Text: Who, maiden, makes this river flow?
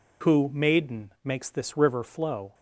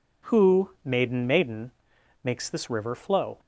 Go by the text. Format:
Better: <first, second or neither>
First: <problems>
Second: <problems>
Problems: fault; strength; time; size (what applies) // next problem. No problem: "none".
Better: first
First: none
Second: says "maiden" twice; at 1.2 s